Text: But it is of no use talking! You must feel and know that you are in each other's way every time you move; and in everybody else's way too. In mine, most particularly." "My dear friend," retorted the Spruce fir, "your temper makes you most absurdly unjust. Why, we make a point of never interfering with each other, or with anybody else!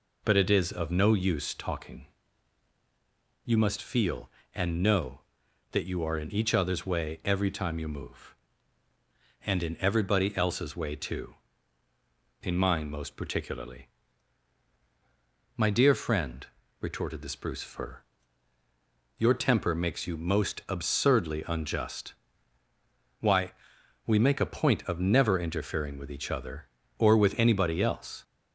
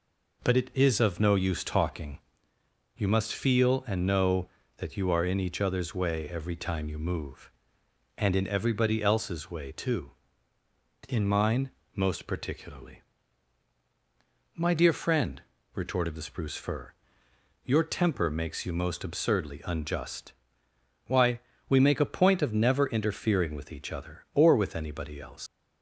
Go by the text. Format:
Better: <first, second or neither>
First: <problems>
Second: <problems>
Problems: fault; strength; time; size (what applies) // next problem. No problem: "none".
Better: first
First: none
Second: leaves "else" unfinished; at 25.4 s; 120 ms